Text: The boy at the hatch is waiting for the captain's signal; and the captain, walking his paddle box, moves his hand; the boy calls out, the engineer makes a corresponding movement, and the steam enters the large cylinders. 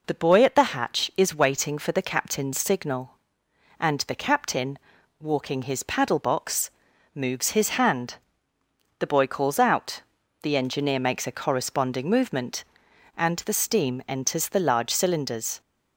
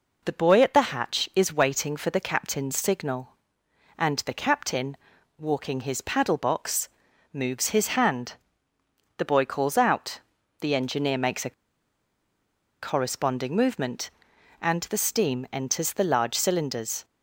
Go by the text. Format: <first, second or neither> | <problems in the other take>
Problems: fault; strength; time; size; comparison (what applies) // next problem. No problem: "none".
first | pauses between "a" and "corresponding"; strong; at 11.5 s; 1.3 s long